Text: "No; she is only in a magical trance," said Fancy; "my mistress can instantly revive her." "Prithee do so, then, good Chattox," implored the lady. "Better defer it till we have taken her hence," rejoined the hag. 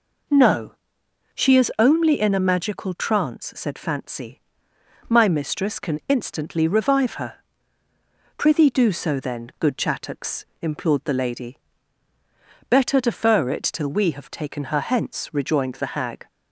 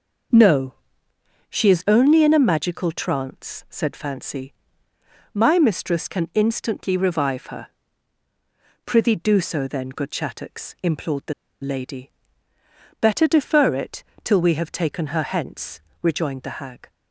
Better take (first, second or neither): first